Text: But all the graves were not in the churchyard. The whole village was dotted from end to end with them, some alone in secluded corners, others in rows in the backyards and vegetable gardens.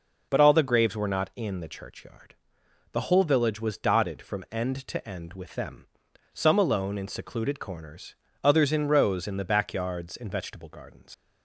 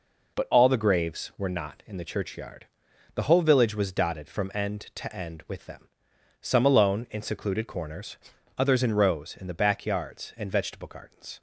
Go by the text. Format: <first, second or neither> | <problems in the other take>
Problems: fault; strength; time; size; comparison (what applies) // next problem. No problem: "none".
second | leaves "gardens" unfinished; at 11.1 s; 80 ms